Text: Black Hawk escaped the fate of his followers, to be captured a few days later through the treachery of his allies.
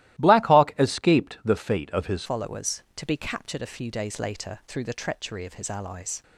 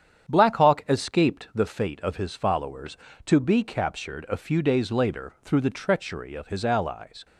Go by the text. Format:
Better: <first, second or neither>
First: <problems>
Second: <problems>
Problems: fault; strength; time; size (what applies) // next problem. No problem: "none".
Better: second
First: starts louder than the rest; strong; until 1.2 s; 15.5 dB // changes voice at "followers"; from 2.2 s on; 4.0 s long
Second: starts louder than the rest; strong; until 1.3 s; 8.5 dB